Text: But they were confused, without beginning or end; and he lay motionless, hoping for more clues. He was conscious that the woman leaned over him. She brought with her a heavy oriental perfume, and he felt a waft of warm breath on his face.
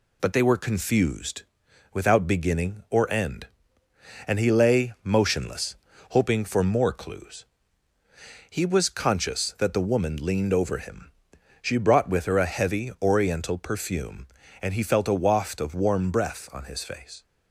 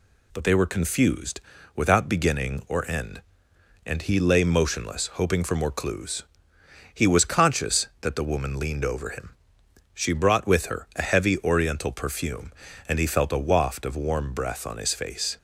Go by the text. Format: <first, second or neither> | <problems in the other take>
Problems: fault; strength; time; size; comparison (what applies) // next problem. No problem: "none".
neither | none